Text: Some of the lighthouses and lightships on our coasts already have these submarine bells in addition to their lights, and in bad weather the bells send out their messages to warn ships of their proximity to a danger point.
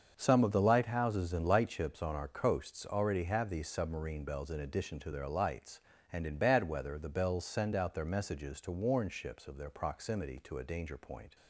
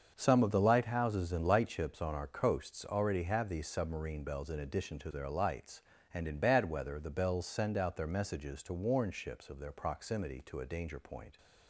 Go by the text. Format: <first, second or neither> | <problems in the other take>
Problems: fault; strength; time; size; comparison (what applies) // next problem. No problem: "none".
neither | starts louder than the rest; the same in both